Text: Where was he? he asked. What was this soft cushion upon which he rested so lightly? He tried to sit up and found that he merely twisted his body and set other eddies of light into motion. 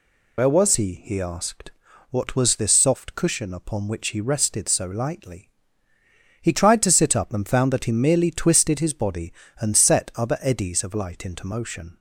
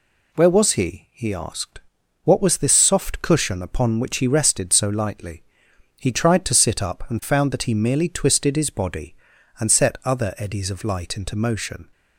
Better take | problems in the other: second | loses the start of "Where"; at 0.3 s; 60 ms

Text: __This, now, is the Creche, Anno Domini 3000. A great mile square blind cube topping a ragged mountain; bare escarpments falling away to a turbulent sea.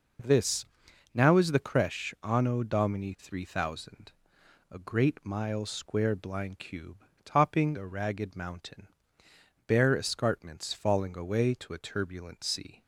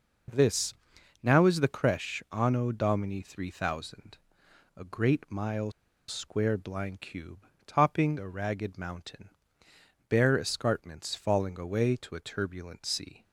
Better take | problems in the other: first | pauses between "mile" and "square"; at 5.7 s; 0.37 s long // pauses between "cube" and "topping"; slight; at 7.4 s; 0.22 s long; slight in the first

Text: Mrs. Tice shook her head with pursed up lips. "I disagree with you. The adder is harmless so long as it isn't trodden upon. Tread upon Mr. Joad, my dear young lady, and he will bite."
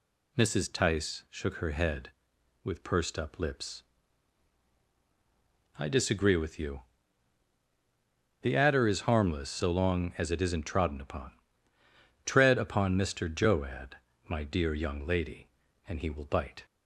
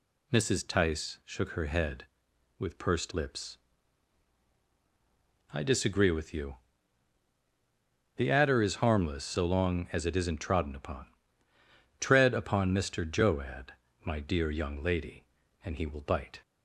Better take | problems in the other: first | skips "up"; at 3.1 s

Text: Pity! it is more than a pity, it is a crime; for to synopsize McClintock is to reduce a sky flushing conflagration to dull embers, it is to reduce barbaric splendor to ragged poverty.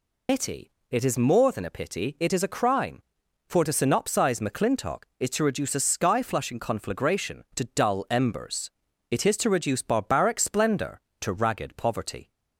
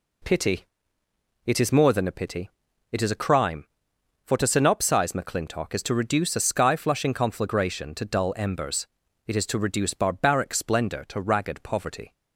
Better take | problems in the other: second | loses the start of "Pity"; at 0.2 s; 130 ms

